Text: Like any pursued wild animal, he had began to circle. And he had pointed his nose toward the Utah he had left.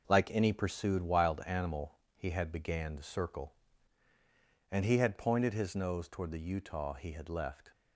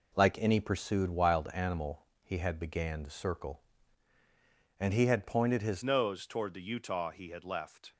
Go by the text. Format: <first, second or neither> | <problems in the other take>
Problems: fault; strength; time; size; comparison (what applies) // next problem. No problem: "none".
first | changes voice at "nose"; from 5.8 s on; 2.1 s long